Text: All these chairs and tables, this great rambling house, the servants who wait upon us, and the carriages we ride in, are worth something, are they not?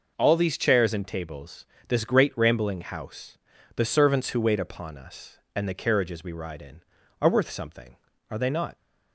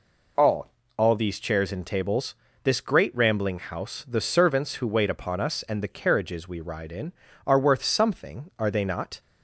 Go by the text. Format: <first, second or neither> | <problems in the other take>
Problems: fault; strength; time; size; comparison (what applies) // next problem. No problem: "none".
first | says "All" twice; at 0.9 s